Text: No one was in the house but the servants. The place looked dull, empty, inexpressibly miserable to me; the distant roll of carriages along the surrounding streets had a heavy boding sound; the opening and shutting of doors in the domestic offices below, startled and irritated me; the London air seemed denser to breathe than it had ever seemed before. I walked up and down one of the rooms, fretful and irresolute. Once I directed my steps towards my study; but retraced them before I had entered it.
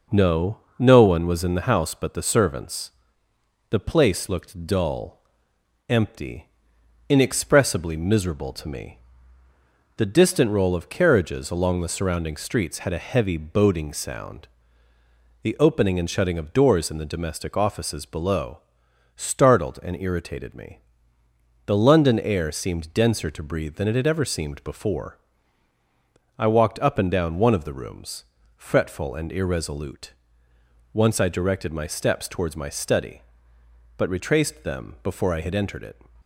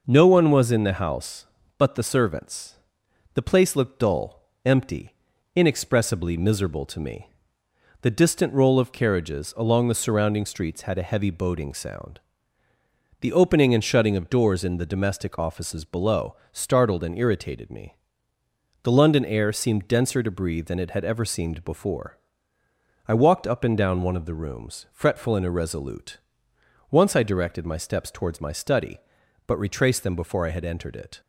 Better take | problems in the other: second | says "No" twice; at 0.7 s

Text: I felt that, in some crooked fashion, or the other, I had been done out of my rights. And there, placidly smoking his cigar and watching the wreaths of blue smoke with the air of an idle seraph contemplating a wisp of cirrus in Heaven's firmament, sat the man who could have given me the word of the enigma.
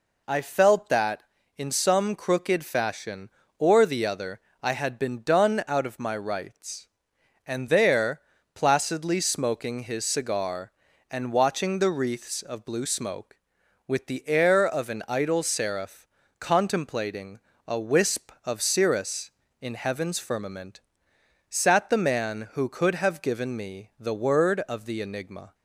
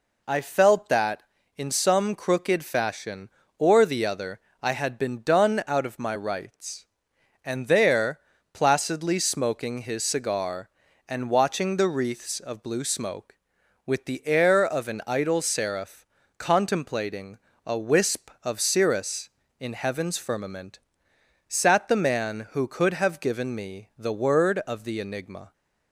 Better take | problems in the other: neither | pauses between "seraph" and "contemplating"; slight; the same in both // pauses between "contemplating" and "a"; slight; the same in both

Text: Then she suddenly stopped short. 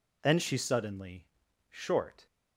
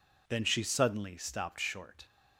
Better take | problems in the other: second | skips "stopped"; at 1.4 s

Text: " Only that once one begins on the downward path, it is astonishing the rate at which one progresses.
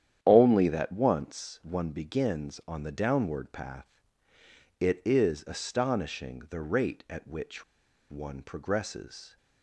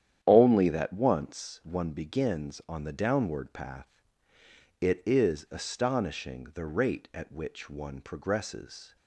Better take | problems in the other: second | starts louder than the rest; strong; until 1.2 s; 10 dB; strong in the second // pauses between "which" and "one"; noticeable; at 7.6 s; 0.47 s long

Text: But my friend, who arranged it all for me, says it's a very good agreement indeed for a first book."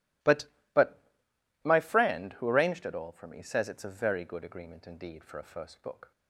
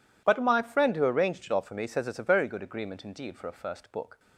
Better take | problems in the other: second | says "But" twice; at 0.7 s

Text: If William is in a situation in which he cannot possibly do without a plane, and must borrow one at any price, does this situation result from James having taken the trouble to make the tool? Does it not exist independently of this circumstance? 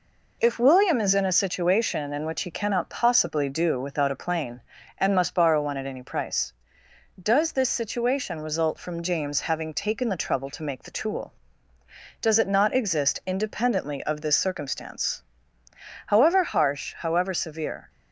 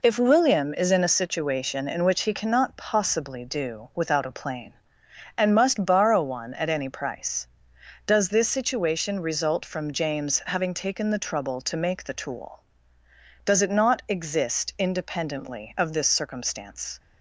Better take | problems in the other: second | goes on to say "However harsh however severe"; strong; from 16.0 s on; 1.8 s long

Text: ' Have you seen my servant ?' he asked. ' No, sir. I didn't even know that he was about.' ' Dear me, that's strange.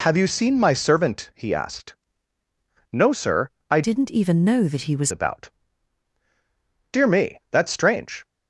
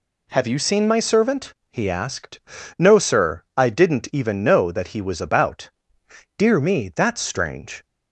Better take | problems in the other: second | changes voice from "didn't" to "was"; from 3.8 to 5.1 s; 1.3 s long

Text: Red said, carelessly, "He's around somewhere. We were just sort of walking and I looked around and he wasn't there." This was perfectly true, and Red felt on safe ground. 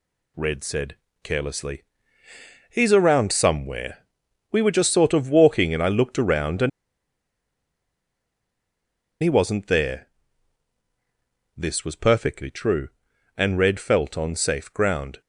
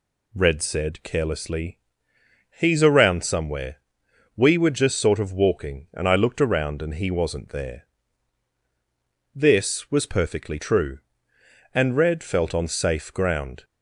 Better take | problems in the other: second | pauses between "and" and "he"; strong; at 6.6 s; 2.5 s long

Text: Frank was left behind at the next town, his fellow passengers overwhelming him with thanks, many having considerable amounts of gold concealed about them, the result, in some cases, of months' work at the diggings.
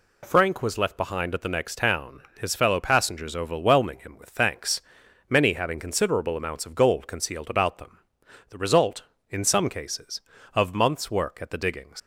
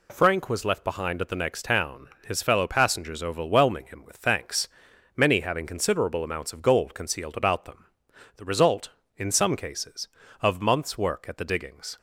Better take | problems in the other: second | leaves "diggings" unfinished; at 11.9 s; 100 ms

